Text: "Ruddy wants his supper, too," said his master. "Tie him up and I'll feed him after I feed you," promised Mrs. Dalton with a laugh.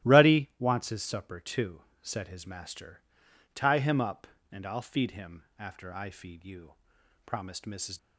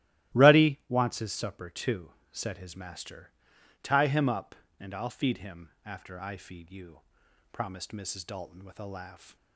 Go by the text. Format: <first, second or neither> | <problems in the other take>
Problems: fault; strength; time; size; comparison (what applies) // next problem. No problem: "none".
second | starts louder than the rest; strong; until 1.1 s; 14 dB; strong in the second // stops before "Dalton with a laugh"; at 7.9 s